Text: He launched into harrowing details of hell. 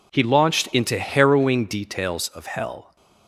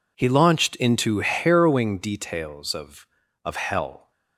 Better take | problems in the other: first | says "of" twice; at 3.4 s

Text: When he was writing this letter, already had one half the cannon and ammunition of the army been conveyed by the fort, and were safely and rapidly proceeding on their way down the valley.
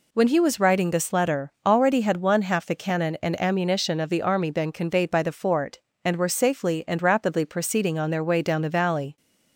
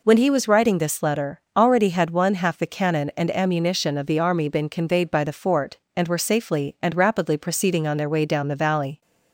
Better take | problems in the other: neither | none

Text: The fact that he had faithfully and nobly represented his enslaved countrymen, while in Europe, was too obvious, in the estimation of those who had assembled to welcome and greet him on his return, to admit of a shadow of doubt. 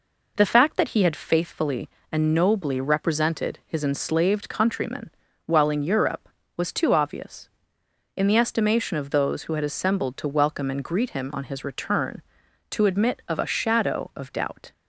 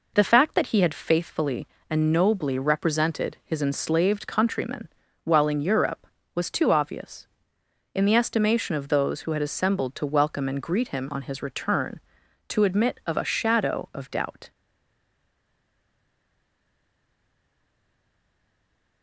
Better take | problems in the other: first | stays silent after the last word; strong; from 14.5 s on; 4.5 s long

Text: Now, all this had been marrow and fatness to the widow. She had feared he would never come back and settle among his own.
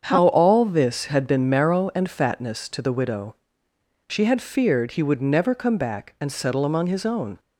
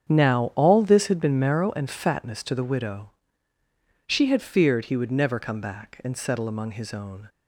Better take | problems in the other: second | starts louder than the rest; strong; until 1.0 s; 7.5 dB; strong in the second // says "How" for "Now"; at 0.0 s

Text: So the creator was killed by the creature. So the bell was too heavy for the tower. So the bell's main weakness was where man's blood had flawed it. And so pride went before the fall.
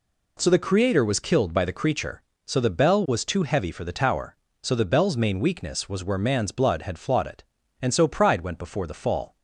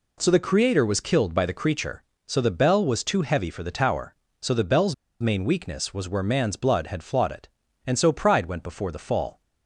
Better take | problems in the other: first | pauses between "bell's" and "main"; slight; at 4.9 s; 0.26 s long

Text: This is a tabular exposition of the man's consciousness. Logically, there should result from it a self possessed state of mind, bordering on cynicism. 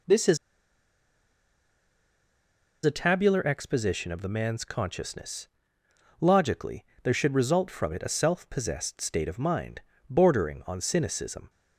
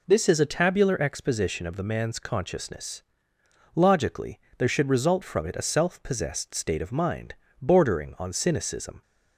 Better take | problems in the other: second | pauses between "is" and "a"; strong; at 0.3 s; 2.4 s long

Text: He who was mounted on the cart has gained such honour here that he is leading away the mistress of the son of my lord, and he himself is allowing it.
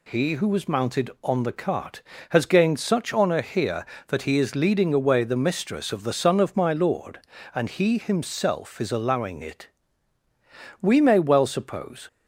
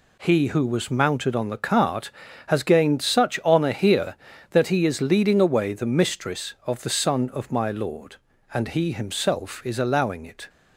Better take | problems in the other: second | goes on to say "We may well suppose"; noticeable; from 10.7 s on; 1.2 s long

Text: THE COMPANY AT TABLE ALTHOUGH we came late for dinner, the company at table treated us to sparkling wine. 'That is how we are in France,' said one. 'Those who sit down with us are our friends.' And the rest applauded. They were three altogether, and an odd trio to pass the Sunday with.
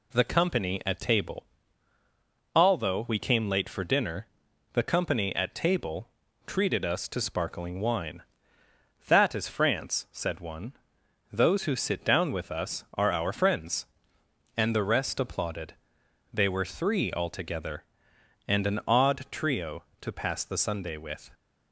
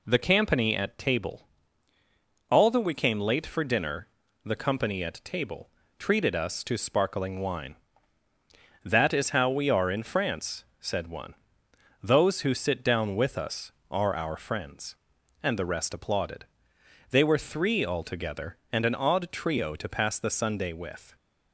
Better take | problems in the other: second | pauses between "TABLE" and "ALTHOUGH"; at 1.4 s; 1.1 s long; also in the second // pauses between "table" and "treated"; at 6.0 s; 0.38 s long; slight in the second // skips "how we are in"; at 9.4 s

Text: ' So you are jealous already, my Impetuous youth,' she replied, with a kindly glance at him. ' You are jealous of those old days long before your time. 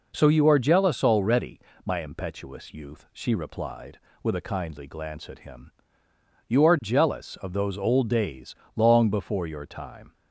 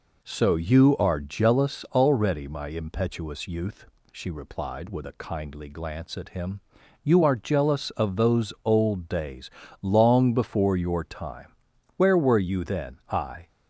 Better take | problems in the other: first | pauses between "days" and "long"; slight; at 9.4 s; 0.32 s long; slight in the first // goes on to say "Where were you then I"; from 11.9 s on; 1.5 s long

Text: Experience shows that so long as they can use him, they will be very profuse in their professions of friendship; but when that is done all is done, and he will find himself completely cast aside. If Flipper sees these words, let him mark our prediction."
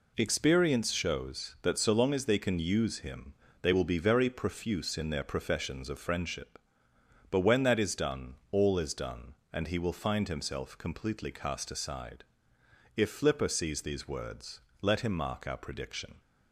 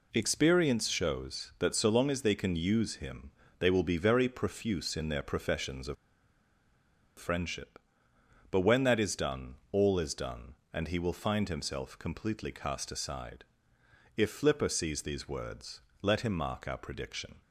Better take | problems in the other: first | pauses between "of" and "friendship"; at 5.9 s; 1.2 s long // pauses between "done" and "all"; slight; at 9.5 s; 0.16 s long; slight in the first

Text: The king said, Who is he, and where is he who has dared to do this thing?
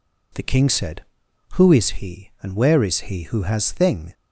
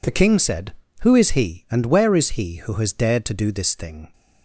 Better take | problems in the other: second | skips "dared to do this"; at 3.7 s

